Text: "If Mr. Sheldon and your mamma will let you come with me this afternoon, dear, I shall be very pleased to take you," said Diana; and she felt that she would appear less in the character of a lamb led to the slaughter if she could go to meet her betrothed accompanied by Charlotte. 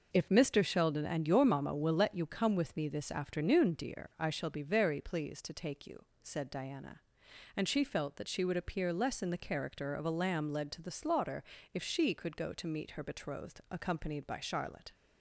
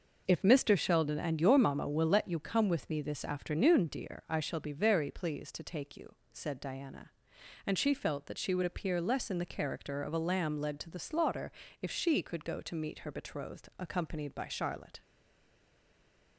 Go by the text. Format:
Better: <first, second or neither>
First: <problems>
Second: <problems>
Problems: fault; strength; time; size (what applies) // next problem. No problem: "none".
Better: first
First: pauses between "slaughter" and "if"; slight; at 11.4 s; 0.30 s long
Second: pauses between "slaughter" and "if"; slight; at 11.5 s; 0.30 s long // stays silent after the last word; noticeable; from 15.0 s on; 1.3 s long